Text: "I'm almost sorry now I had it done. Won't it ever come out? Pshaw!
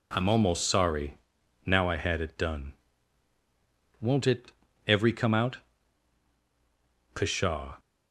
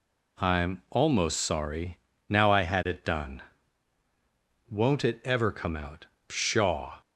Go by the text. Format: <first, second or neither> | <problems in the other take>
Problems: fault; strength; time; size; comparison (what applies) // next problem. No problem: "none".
second | pauses between "sorry" and "now"; noticeable; at 1.1 s; 0.48 s long; slight in the second // says "every" for "ever"; at 4.8 s